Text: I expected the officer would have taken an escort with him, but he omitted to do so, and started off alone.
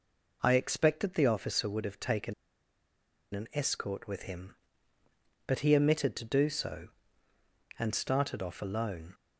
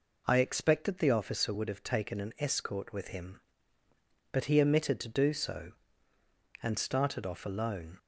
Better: second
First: pauses between "taken" and "an"; at 2.3 s; 1.0 s long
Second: none

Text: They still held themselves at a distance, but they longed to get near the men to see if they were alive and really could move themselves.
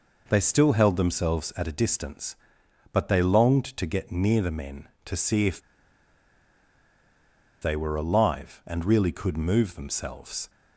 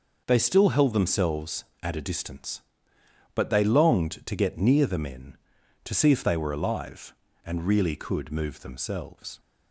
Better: second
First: pauses between "if" and "they"; strong; at 5.6 s; 2.0 s long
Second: none

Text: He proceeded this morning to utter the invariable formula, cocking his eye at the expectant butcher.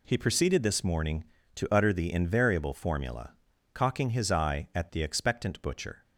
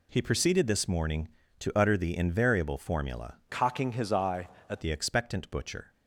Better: first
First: none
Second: changes voice from "cocking" to "at"; from 3.4 to 4.8 s; 1.4 s long

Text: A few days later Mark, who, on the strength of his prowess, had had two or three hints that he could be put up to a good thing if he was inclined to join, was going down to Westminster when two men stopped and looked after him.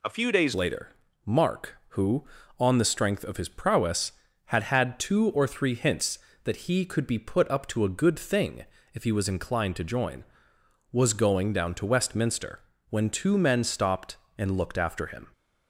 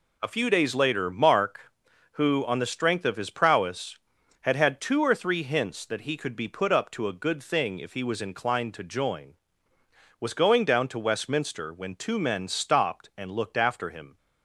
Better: second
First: changes voice at "later"; from 0.5 s on; 14.8 s long // pauses between "later" and "Mark"; slight; at 0.8 s; 0.36 s long // pauses between "thing" and "if"; slight; at 8.6 s; 0.30 s long // pauses between "Westminster" and "when"; slight; at 12.5 s; 0.28 s long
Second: none

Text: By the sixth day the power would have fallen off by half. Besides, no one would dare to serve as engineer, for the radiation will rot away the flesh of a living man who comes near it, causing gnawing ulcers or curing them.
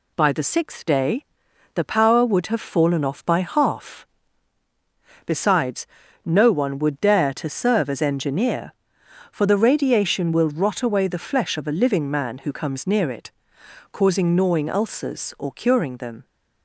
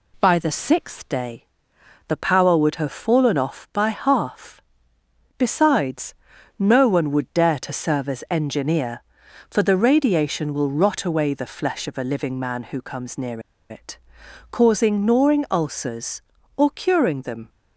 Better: first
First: pauses between "day" and "the"; noticeable; at 1.2 s; 0.48 s long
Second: pauses between "day" and "the"; noticeable; at 1.4 s; 0.62 s long // pauses between "near" and "it"; slight; at 13.4 s; 0.29 s long

